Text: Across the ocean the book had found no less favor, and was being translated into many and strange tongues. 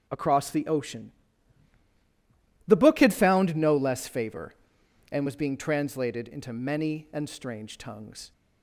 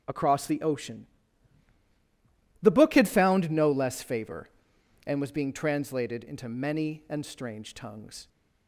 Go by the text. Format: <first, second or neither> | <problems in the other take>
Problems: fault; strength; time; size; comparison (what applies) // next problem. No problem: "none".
neither | starts louder than the rest; the same in both // pauses between "ocean" and "the"; strong; the same in both